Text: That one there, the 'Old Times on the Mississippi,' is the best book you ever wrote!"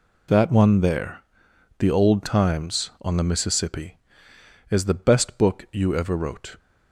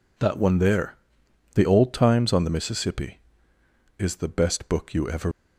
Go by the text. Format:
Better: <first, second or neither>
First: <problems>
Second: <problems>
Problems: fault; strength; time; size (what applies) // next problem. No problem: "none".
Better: first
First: none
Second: stops before "wrote"; at 5.3 s